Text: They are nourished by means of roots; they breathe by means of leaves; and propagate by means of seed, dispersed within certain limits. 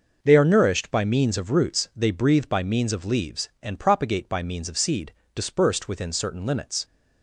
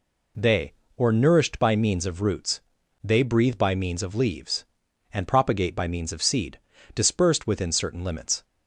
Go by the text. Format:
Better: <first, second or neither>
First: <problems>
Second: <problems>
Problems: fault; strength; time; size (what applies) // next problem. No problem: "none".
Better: first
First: none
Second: says "or" for "are"; at 0.9 s